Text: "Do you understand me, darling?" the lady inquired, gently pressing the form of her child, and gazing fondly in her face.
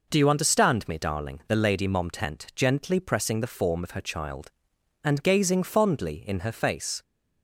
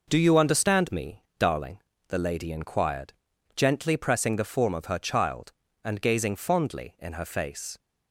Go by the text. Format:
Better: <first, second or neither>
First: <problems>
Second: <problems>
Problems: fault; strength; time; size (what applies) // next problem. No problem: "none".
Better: second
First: says "momtent" for "inquired"; at 1.8 s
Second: none